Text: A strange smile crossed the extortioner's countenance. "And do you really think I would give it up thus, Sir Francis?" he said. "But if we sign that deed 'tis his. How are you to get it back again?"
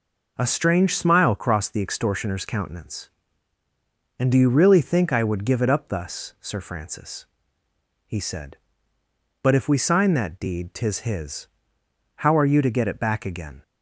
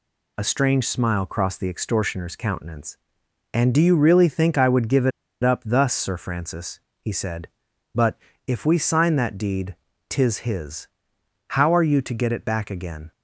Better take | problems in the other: first | pauses between "it" and "up"; slight; at 5.1 s; 0.32 s long // pauses between "But" and "if"; slight; at 8.1 s; 0.30 s long // pauses between "deed" and "tis"; slight; at 9.7 s; 0.32 s long

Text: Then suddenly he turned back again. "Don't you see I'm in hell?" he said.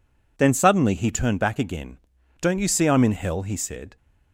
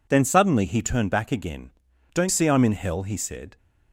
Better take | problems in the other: first | skips "you"; at 2.2 s

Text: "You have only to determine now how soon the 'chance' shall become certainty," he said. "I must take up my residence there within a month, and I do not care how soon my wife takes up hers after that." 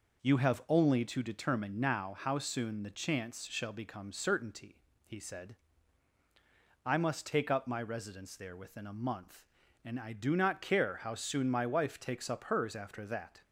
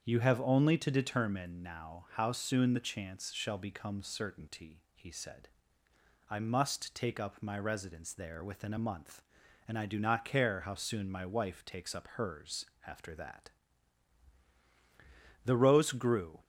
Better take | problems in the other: first | starts louder than the rest; strong; until 1.0 s; 7.5 dB // pauses between "hers" and "after"; slight; at 12.6 s; 0.22 s long // goes on to say "The rose grew"; noticeable; from 15.4 s on; 1.0 s long

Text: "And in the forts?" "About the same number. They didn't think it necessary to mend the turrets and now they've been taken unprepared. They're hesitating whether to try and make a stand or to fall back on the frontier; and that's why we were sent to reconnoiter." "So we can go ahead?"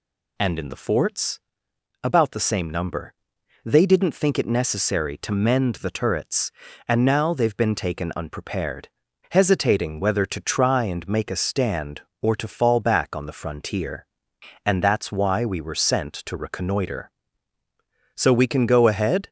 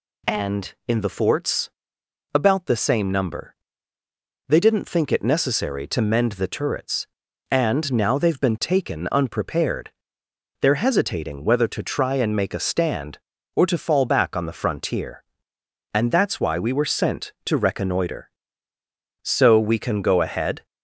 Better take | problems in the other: second | skips "They're"; at 9.0 s

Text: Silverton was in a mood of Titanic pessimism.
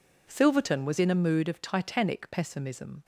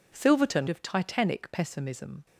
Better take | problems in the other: first | skips "was in a mood"; at 0.6 s

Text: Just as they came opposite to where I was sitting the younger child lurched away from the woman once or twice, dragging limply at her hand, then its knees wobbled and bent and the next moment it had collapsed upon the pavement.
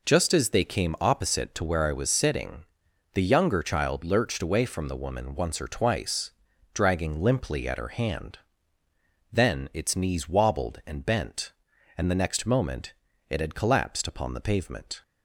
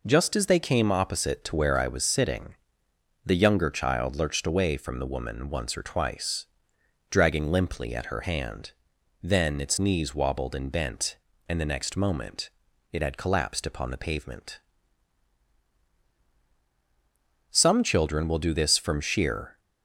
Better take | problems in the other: first | pauses between "sitting" and "the"; noticeable; at 2.5 s; 0.70 s long; noticeable in the first // pauses between "moment" and "it"; at 12.4 s; 0.44 s long; slight in the first // goes on to say "Some children will do this from sheer"; strong; from 17.5 s on; 2.0 s long

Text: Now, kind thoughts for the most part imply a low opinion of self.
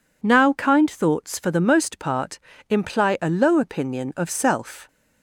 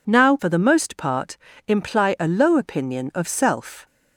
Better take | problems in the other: first | skips "kind thoughts"; at 0.3 s // pauses between "part" and "imply"; slight; at 1.3 s; 0.30 s long; slight in the first

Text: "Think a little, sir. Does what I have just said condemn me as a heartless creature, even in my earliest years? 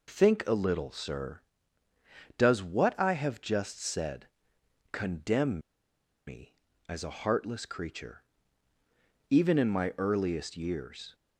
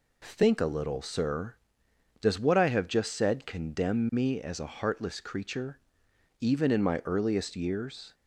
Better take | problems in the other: second | pauses between "said" and "condemn"; noticeable; at 4.2 s; 0.64 s long // pauses between "condemn" and "me"; noticeable; at 5.5 s; 0.68 s long

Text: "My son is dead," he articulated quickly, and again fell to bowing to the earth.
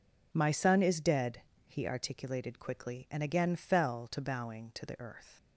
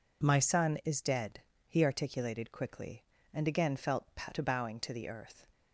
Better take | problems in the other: first | says "felt" for "fell"; at 3.7 s

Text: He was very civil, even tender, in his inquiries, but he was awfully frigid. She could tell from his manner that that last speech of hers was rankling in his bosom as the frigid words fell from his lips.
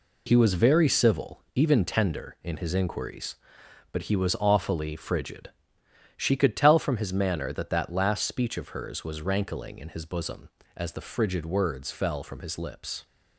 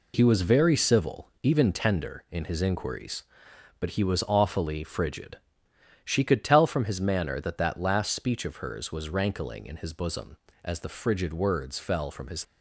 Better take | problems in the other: first | stops before "lips"; at 12.4 s

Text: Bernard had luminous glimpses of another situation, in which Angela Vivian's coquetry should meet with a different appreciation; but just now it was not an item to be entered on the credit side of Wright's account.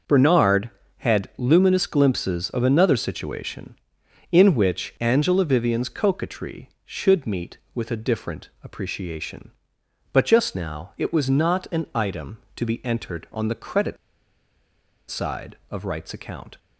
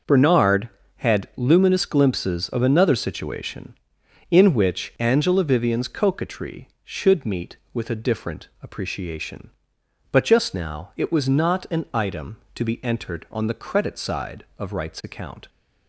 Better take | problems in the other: second | pauses between "credit" and "side"; at 13.9 s; 1.1 s long

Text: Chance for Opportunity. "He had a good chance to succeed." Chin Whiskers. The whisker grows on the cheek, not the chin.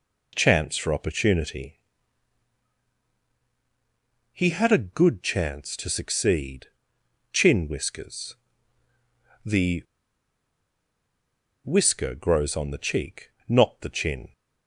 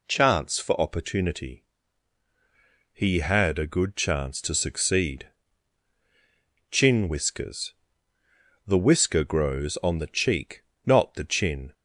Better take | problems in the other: second | pauses between "The" and "whisker"; strong; at 9.8 s; 1.8 s long

